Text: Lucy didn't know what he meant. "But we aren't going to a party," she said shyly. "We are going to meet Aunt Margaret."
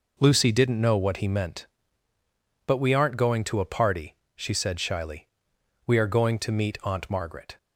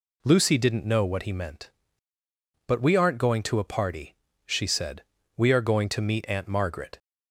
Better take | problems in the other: first | skips "shyly"; at 5.2 s

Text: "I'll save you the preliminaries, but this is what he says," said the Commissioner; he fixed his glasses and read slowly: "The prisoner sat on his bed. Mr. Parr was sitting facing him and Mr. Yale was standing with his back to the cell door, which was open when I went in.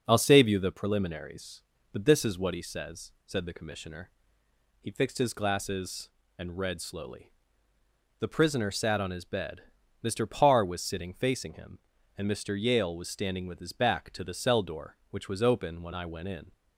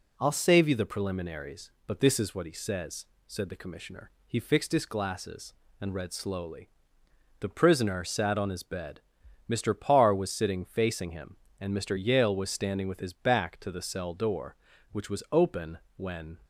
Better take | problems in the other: first | pauses between "open" and "when"; slight; at 15.7 s; 0.18 s long // stops before "I went in"; at 16.4 s

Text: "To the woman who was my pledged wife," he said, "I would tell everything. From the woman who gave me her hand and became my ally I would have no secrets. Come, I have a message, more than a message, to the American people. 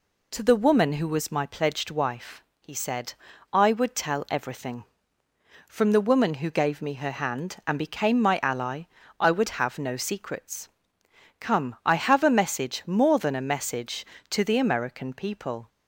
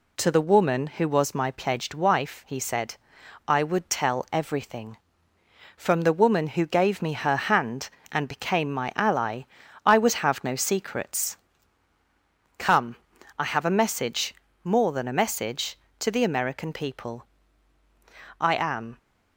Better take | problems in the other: first | pauses between "ally" and "I"; at 9.4 s; 0.42 s long; slight in the first // goes on to say "I am"; from 18.3 s on; 0.58 s long

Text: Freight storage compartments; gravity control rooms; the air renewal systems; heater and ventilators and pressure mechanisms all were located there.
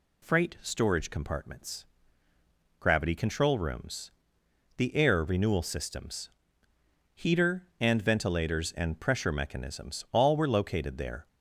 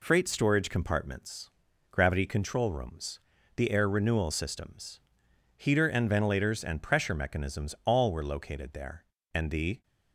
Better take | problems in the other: first | goes on to say "And the"; from 9.3 s on; 0.50 s long

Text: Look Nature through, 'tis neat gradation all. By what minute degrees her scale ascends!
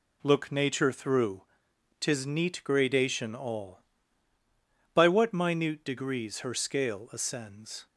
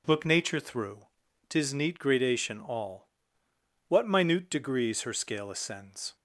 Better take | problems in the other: first | skips "By"; at 3.4 s

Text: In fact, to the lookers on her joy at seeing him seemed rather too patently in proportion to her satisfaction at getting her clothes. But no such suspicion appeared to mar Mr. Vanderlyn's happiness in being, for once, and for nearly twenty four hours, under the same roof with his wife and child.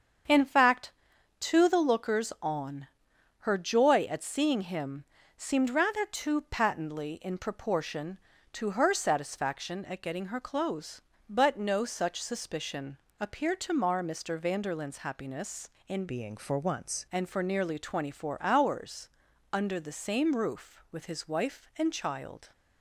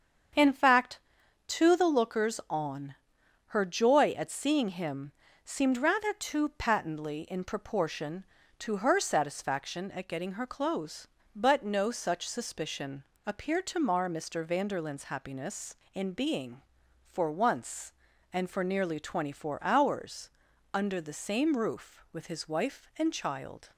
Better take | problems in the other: second | starts louder than the rest; strong; until 1.7 s; 7.5 dB; strong in the second // pauses between "on" and "her"; noticeable; at 2.8 s; 0.52 s long; noticeable in the second // pauses between "him" and "seemed"; slight; at 5.0 s; 0.32 s long; slight in the second // pauses between "suspicion" and "appeared"; slight; at 12.9 s; 0.24 s long; slight in the second // changes voice from "being" to "once"; from 16.0 to 17.0 s; 1.0 s long

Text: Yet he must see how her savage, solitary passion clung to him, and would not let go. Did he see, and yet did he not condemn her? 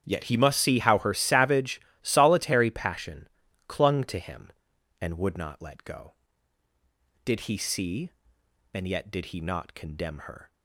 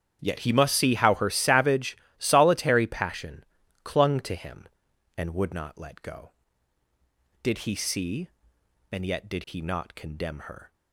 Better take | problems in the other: neither | starts louder than the rest; strong; the same in both // pauses between "passion" and "clung"; the same in both

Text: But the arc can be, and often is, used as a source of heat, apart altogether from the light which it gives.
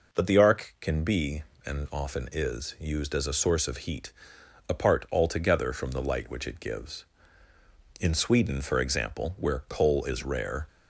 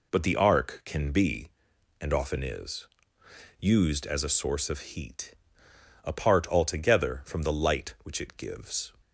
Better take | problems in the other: second | goes on to say "In Sweden for example where coal is rare"; strong; from 7.9 s on; 2.6 s long

